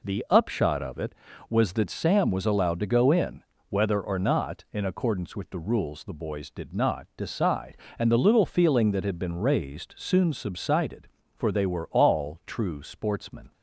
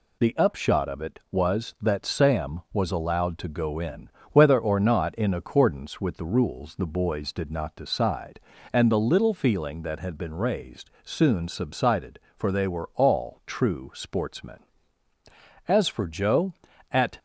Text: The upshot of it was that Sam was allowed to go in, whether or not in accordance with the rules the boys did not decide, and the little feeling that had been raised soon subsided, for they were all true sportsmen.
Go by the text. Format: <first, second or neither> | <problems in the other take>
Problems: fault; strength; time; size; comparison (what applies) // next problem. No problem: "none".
first | goes on to say "As for Joe at"; from 15.6 s on; 1.5 s long